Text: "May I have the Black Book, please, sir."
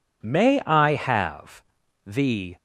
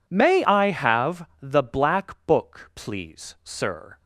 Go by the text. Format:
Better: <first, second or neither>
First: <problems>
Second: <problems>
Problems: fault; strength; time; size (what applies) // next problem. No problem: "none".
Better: second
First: pauses between "have" and "the"; at 1.6 s; 0.44 s long // stops before "Black Book please sir"; at 2.5 s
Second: pauses between "have" and "the"; slight; at 1.2 s; 0.16 s long